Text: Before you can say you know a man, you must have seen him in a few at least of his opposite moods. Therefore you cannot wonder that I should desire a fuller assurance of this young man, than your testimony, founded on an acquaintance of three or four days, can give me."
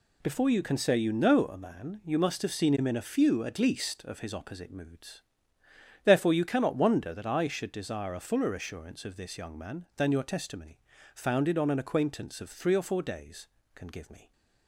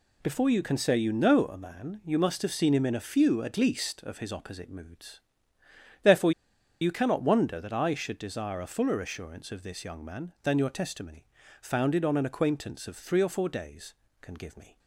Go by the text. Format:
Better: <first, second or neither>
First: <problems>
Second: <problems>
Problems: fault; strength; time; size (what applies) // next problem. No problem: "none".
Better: first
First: none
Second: pauses between "Therefore" and "you"; noticeable; at 6.3 s; 0.50 s long